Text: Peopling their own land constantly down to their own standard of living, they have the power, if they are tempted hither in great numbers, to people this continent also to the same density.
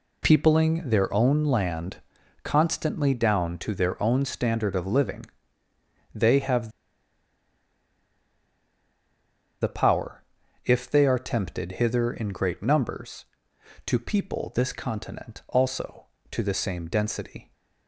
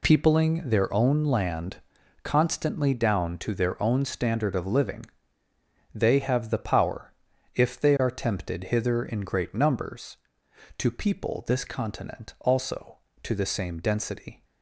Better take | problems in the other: second | pauses between "land" and "constantly"; noticeable; at 1.9 s; 0.46 s long; noticeable in the second // pauses between "have" and "the"; strong; at 6.6 s; 2.9 s long

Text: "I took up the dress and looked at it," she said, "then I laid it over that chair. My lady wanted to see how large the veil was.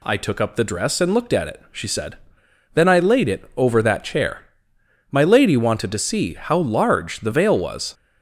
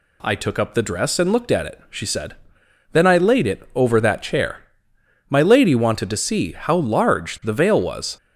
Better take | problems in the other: neither | none

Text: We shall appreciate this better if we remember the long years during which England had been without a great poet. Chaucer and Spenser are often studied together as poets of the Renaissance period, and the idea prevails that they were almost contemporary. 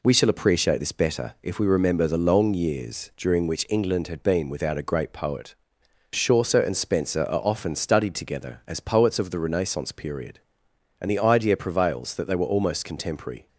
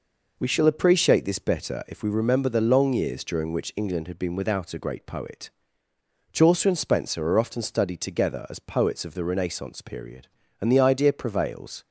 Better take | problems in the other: first | stops before "that they were almost contemporary"; at 11.8 s

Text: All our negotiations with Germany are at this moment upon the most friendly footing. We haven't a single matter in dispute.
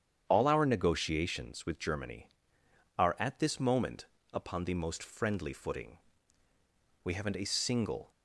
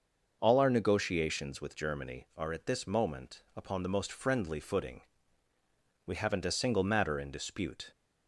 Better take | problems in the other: second | starts louder than the rest; strong; until 1.2 s; 8.5 dB // pauses between "moment" and "upon"; slight; at 4.0 s; 0.26 s long // stops before "matter in dispute"; at 8.1 s

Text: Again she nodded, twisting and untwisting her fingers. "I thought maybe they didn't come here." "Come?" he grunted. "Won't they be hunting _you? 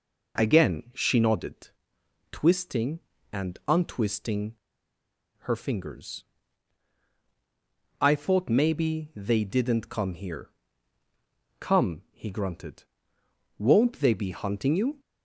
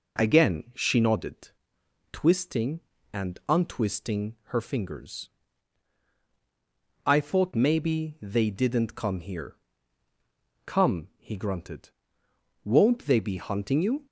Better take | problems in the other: second | pauses between "untwisting" and "her"; noticeable; at 4.5 s; 0.85 s long

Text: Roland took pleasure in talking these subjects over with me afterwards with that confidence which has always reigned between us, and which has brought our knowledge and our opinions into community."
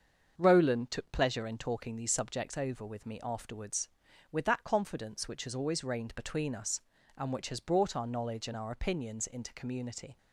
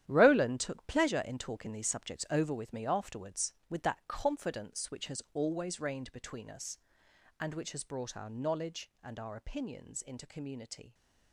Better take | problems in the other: first | gets quieter; strong; throughout; 10.5 dB // starts louder than the rest; strong; until 1.0 s; 11 dB; also in the first

